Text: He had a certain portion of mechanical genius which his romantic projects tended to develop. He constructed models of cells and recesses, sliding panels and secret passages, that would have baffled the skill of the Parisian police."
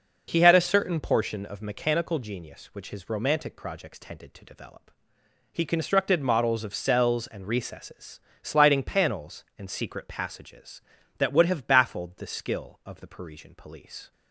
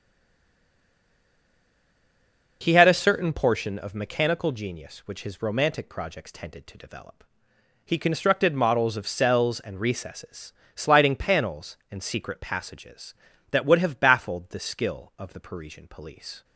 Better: first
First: none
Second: stays silent before the first word; strong; until 2.6 s; 2.6 s long

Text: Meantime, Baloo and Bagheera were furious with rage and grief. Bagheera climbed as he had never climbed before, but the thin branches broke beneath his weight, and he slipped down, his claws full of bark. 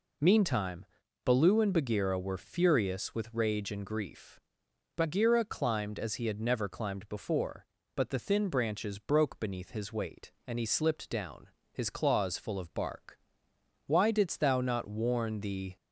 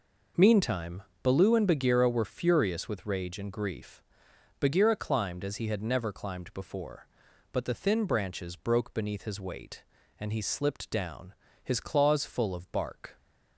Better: second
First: goes on to say "Why didst thou not warn the"; strong; from 13.8 s on; 1.8 s long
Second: none

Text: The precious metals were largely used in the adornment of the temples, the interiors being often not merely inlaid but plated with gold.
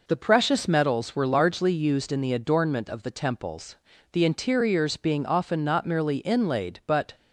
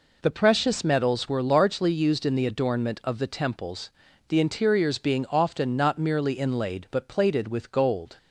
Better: second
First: stops before "plated with gold"; at 7.1 s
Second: none

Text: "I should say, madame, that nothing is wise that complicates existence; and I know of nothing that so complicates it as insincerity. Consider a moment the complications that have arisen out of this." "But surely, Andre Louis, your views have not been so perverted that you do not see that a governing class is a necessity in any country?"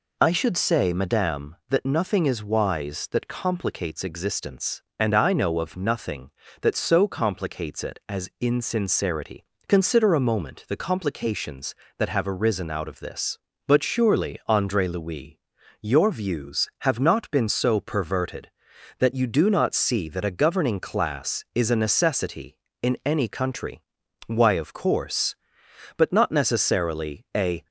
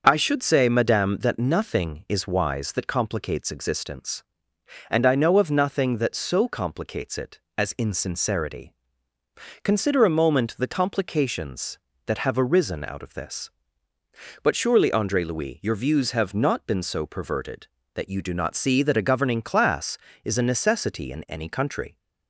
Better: second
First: goes on to say "Why of course But not necessarily a"; strong; from 24.2 s on; 3.4 s long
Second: none

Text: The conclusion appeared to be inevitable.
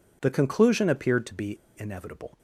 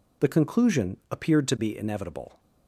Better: second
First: pauses between "be" and "inevitable"; slight; at 1.5 s; 0.23 s long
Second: none

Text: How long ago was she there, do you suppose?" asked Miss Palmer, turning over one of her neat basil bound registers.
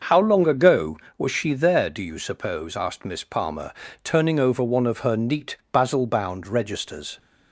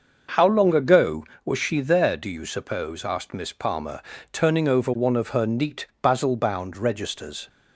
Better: neither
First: starts louder than the rest; noticeable; until 1.2 s; 6 dB // pauses between "neat" and "basil"; slight; at 5.5 s; 0.16 s long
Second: starts louder than the rest; until 1.5 s; 6 dB // pauses between "neat" and "basil"; slight; at 5.8 s; 0.16 s long

